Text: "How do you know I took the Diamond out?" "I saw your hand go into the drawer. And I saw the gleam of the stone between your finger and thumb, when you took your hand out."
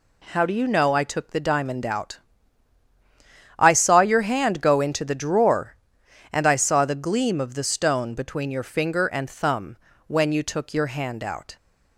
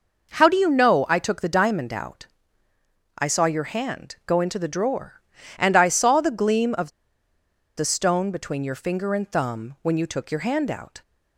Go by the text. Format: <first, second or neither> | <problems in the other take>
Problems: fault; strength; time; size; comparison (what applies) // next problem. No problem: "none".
first | pauses between "of" and "the"; noticeable; at 6.8 s; 0.88 s long